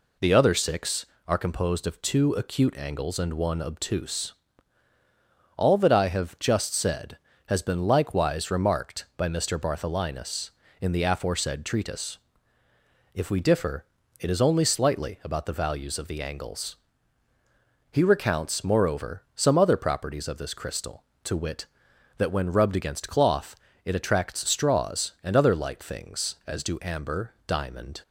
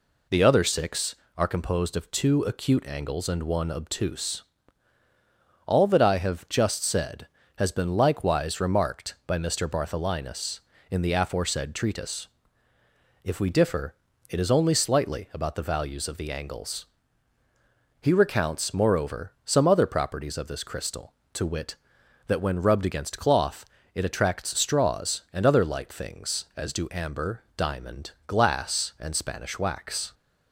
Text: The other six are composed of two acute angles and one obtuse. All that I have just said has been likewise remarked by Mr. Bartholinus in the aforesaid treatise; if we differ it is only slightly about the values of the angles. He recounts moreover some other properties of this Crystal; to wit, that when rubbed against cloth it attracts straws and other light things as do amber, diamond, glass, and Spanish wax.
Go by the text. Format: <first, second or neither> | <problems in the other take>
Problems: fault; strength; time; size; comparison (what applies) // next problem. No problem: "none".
second | pauses between "differ" and "it"; slight; at 13.8 s; 0.36 s long; slight in the second // pauses between "cloth" and "it"; slight; at 23.5 s; 0.28 s long; slight in the second // stops before "glass and Spanish wax"; at 28.0 s